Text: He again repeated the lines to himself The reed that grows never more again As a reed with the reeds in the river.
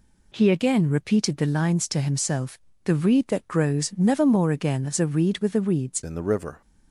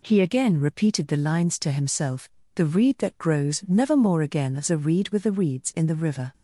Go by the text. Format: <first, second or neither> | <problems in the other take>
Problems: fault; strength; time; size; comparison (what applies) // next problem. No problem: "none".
second | pauses between "himself" and "The"; slight; at 2.5 s; 0.28 s long; slight in the second // changes voice at "in"; from 6.0 s on; 0.6 s long